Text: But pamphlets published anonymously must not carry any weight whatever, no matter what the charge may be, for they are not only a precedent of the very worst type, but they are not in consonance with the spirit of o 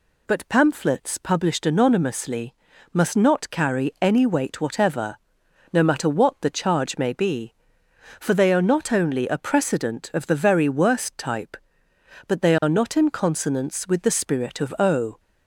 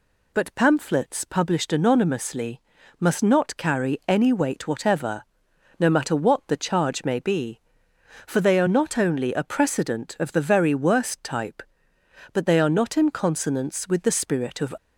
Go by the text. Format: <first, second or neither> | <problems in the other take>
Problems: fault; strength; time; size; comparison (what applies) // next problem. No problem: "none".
first | pauses between "anonymously" and "must"; slight; at 2.6 s; 0.36 s long; slight in the first // stops before "o"; at 14.7 s